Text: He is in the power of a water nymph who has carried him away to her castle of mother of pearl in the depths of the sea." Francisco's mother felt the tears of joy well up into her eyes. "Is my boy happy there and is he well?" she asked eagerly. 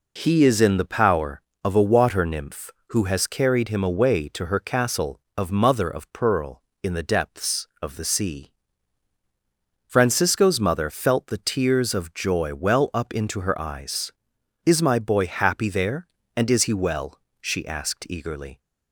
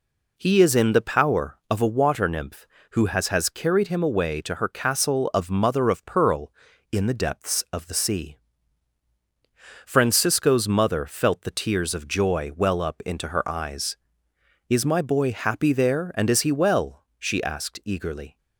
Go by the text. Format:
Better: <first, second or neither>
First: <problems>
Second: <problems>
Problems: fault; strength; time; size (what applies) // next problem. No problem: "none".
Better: first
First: none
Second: says "has" twice; at 3.2 s